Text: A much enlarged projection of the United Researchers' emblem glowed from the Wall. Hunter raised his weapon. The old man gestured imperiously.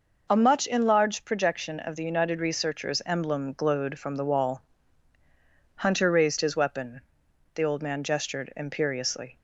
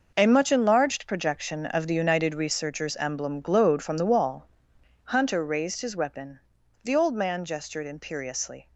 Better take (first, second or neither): first